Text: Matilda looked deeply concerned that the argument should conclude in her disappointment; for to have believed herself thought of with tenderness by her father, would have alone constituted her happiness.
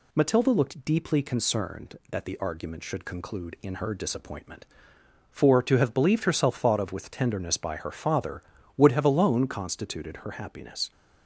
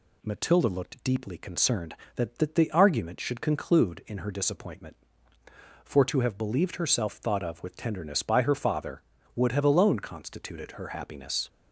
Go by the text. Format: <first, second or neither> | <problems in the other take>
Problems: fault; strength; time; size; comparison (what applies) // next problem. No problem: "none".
first | says "that" twice; at 2.3 s